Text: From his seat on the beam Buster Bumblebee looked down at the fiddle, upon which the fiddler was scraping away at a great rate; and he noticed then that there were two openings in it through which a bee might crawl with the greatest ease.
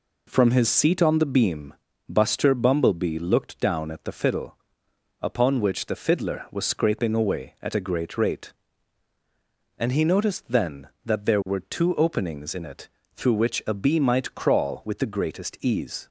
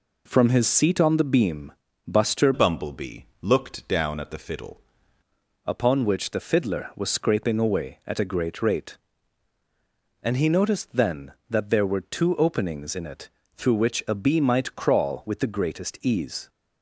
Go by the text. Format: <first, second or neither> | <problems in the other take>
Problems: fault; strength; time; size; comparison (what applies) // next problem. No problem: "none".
first | pauses between "beam" and "Buster"; slight; at 1.7 s; 0.34 s long; slight in the first // changes voice from "Bumblebee" to "fiddle"; from 2.5 to 4.8 s; 2.3 s long // pauses between "Bumblebee" and "looked"; slight; at 3.2 s; 0.18 s long // pauses between "it" and "through"; slight; at 13.2 s; 0.26 s long; slight in the first